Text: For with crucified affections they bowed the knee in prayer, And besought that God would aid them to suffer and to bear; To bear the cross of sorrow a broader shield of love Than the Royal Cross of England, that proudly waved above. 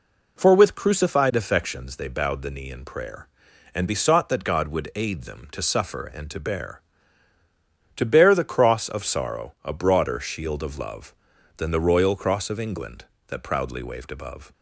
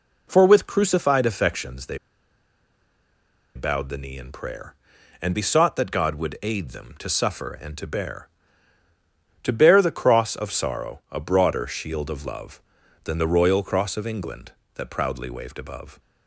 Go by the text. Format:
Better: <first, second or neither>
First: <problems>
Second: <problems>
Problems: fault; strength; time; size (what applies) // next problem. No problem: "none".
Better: first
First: none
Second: pauses between "they" and "bowed"; strong; at 1.9 s; 1.5 s long